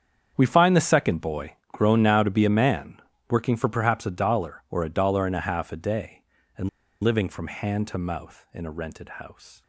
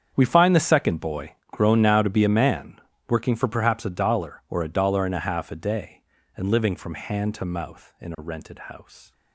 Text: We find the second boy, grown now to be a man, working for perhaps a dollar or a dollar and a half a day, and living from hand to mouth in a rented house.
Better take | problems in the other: second | starts louder than the rest; strong; until 1.3 s; 8 dB; strong in the second // pauses between "and" and "living"; slight; at 6.6 s; 0.34 s long

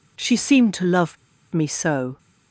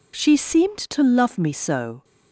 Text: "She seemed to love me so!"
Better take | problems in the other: second | pauses between "love" and "me"; at 1.1 s; 0.36 s long

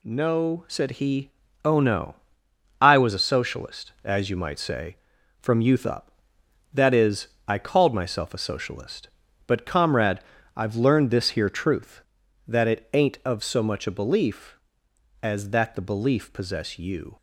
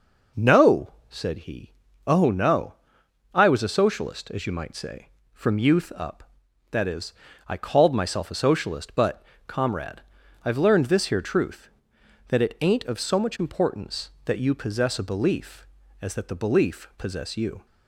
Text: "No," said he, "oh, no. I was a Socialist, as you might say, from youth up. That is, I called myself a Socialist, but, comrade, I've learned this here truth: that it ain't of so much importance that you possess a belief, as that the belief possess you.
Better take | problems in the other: second | skips "importance that you possess"; at 13.8 s

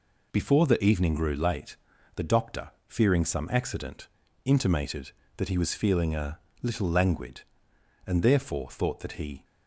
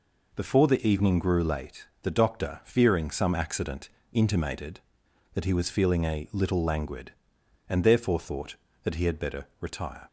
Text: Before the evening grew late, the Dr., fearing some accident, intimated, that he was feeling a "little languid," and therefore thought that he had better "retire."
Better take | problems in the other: second | pauses between "a" and "little"; slight; at 6.3 s; 0.24 s long // stops before "had better retire"; at 9.4 s

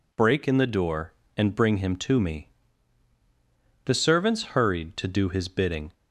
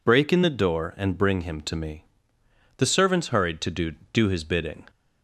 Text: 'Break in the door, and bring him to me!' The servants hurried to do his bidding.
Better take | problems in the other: first | says "do" twice; at 4.1 s

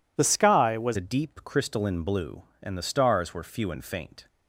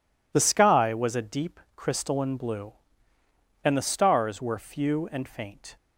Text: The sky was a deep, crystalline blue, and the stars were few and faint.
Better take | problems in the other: second | changes voice at "a"; from 0.9 s on; 3.3 s long

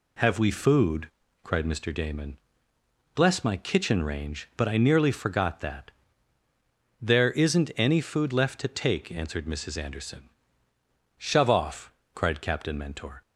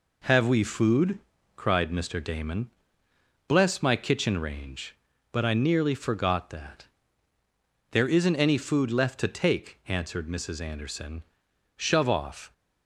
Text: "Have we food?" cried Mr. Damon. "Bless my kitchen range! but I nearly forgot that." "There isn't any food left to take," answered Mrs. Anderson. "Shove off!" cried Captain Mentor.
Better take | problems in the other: first | stops before "cried Captain Mentor"; at 12.5 s

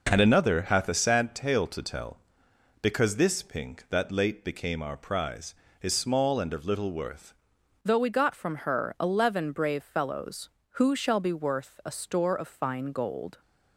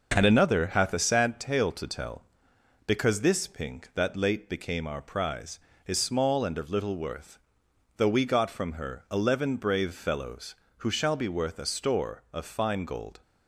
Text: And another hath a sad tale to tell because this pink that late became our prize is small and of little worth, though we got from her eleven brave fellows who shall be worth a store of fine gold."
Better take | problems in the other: second | changes voice at "though"; from 7.8 s on; 5.5 s long

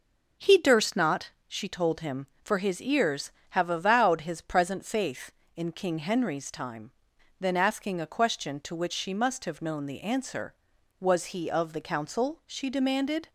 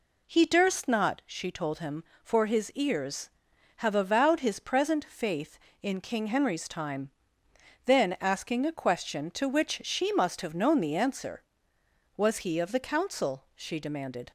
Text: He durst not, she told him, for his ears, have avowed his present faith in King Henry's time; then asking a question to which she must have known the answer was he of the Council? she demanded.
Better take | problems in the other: neither | none

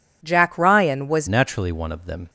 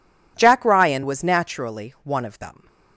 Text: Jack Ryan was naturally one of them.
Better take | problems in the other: second | changes voice at "naturally"; from 1.2 s on; 1.0 s long

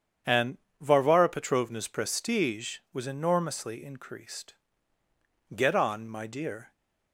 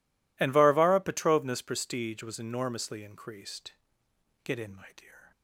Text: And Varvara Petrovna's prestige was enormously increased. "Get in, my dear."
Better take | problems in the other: second | starts louder than the rest; strong; until 1.5 s; 8 dB // pauses between "And" and "Varvara"; slight; at 0.5 s; 0.23 s long // says "on" for "in"; at 5.7 s

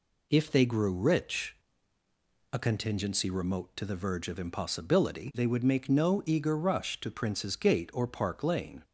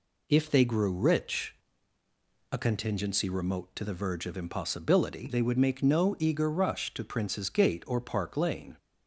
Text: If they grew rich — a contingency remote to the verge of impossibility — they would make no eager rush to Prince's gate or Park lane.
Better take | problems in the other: neither | none

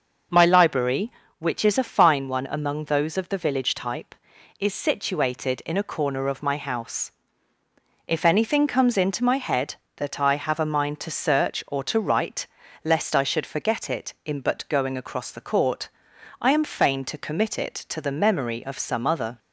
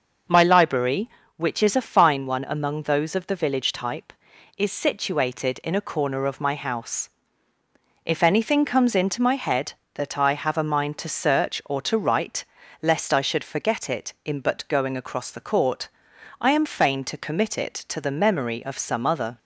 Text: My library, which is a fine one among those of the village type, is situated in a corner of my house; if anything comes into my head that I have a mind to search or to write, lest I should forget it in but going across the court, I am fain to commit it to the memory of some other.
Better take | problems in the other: neither | none

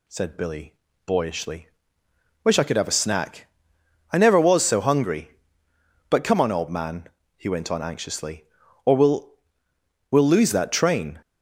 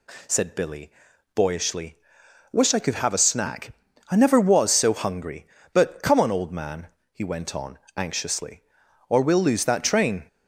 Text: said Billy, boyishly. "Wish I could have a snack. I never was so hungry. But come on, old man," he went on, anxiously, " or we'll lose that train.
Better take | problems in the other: second | says "we'll" twice; at 10.1 s

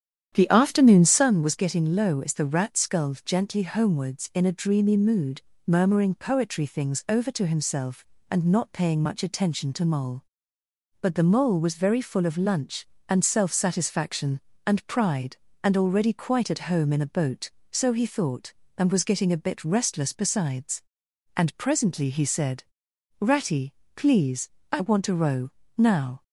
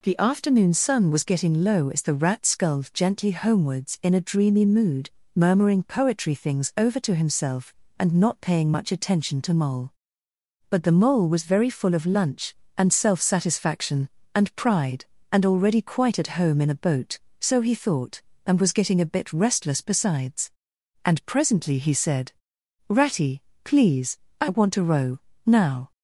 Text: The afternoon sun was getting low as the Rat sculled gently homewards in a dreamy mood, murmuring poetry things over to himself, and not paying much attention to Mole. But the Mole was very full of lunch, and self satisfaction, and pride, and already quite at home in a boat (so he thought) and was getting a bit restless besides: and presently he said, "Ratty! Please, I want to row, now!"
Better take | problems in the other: second | starts louder than the rest; strong; until 1.3 s; 9.5 dB

